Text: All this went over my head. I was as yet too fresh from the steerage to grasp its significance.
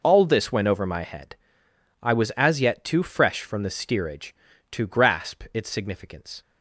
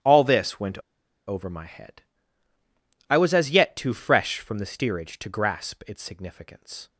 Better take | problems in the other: first | starts louder than the rest; strong; until 1.5 s; 11 dB // pauses between "went" and "over"; noticeable; at 0.7 s; 0.48 s long

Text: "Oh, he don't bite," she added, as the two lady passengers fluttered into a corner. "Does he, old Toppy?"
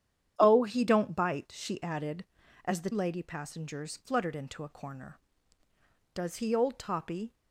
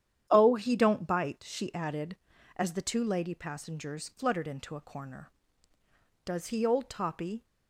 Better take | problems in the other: second | starts louder than the rest; strong; until 1.3 s; 9.5 dB; strong in the second // skips "two"; at 2.9 s

